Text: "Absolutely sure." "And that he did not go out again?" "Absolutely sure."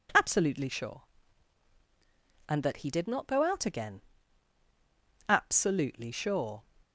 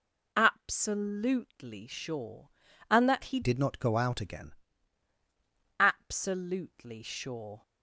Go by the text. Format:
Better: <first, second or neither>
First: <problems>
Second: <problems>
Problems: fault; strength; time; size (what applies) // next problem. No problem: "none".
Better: first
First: none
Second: changes voice from "did" to "again"; from 3.4 to 4.5 s; 1.1 s long